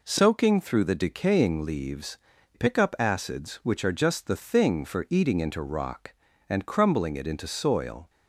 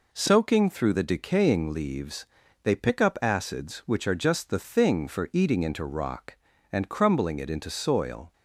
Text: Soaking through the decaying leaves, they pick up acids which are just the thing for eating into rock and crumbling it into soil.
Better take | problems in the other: second | skips "they"; at 2.3 s

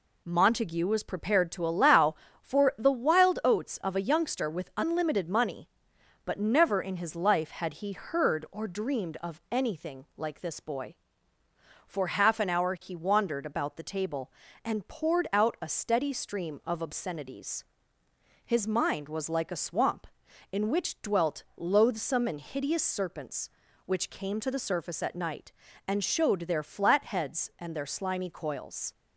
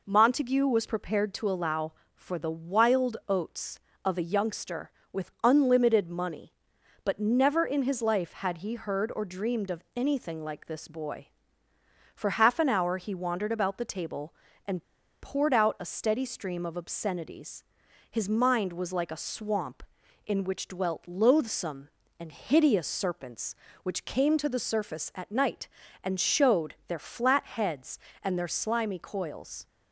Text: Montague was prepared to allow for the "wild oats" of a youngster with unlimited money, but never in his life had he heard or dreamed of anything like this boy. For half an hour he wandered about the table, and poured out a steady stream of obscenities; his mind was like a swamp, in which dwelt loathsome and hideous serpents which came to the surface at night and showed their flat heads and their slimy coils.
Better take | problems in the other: first | pauses between "and" and "poured"; at 14.8 s; 0.39 s long

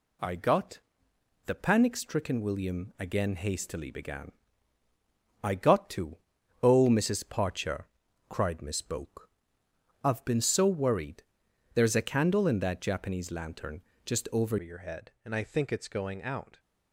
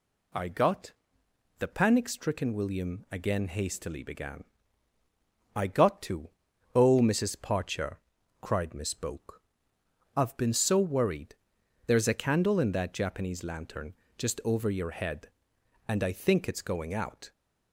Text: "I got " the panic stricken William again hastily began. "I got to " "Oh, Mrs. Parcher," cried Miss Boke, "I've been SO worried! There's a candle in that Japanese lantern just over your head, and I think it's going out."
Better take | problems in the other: second | pauses between "lantern" and "just"; slight; at 13.8 s; 0.22 s long; slight in the second // changes voice at "your"; from 14.6 s on; 1.9 s long

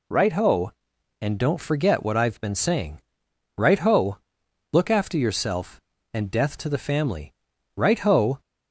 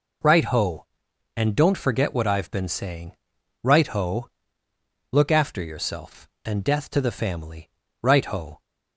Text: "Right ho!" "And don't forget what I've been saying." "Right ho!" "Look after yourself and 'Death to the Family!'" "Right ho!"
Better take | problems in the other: neither | none

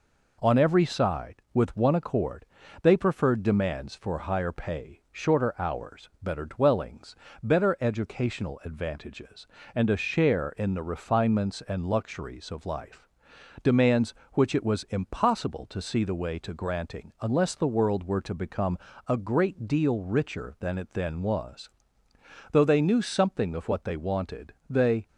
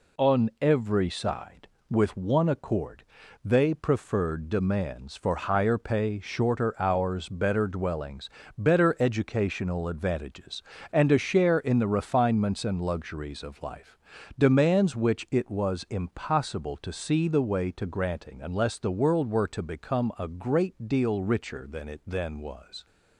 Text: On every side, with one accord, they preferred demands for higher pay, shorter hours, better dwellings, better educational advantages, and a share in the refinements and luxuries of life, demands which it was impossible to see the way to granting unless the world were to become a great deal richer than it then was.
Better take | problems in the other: second | pauses between "become" and "a"; slight; at 18.7 s; 0.30 s long // goes on to say "Though they knew something of what they wanted they"; strong; from 22.5 s on; 2.5 s long

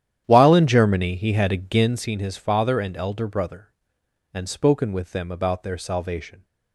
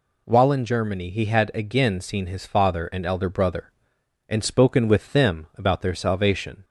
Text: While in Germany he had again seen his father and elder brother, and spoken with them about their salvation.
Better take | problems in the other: second | starts louder than the rest; strong; until 2.1 s; 10.5 dB

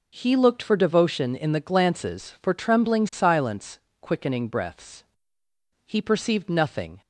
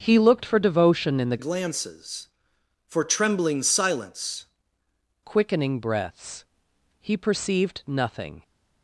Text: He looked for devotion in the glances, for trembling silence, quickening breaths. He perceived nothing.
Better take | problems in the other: first | starts louder than the rest; until 1.0 s; 6.5 dB // changes voice from "glances" to "silence"; from 1.3 to 4.4 s; 3.1 s long

